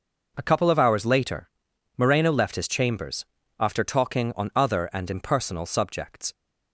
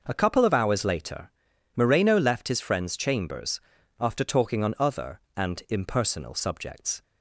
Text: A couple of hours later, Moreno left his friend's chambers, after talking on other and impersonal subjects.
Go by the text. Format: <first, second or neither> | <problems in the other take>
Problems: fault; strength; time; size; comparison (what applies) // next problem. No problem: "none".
second | skips "friend's"; at 2.6 s